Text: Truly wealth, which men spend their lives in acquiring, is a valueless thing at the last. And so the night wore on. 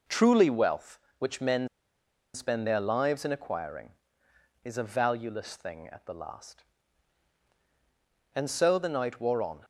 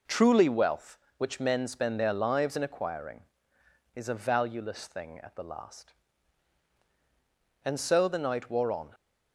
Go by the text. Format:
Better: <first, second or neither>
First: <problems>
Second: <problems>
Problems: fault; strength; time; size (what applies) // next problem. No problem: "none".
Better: second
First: pauses between "men" and "spend"; noticeable; at 1.6 s; 0.66 s long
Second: none